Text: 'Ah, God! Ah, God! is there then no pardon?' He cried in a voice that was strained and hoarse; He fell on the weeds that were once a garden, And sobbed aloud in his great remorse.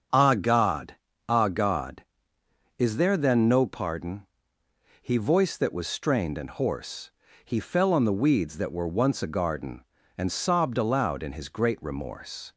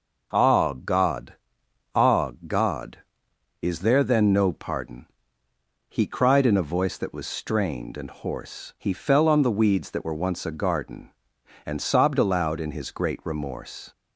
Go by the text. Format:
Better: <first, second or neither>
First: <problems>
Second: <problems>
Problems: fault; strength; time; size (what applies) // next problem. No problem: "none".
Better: second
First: starts louder than the rest; strong; until 1.4 s; 7 dB // skips "cried in a"; at 5.1 s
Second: none